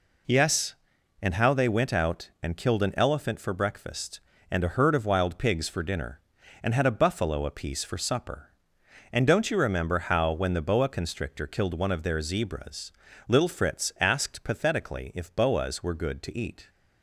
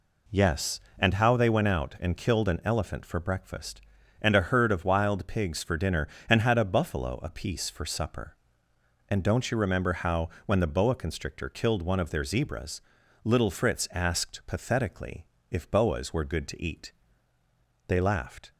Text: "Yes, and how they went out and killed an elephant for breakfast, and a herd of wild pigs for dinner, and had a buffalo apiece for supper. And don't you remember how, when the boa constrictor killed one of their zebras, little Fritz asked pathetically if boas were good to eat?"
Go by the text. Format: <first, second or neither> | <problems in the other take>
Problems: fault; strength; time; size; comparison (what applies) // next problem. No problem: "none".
first | pauses between "pathetically" and "if"; slight; at 15.2 s; 0.24 s long // goes on to say "They laughed"; noticeable; from 17.8 s on; 0.64 s long